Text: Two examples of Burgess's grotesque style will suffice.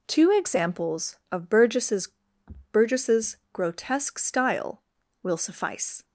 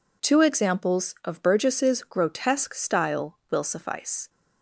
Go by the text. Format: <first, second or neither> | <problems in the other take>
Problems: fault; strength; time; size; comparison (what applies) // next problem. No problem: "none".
second | says "Burgess's" twice; at 2.7 s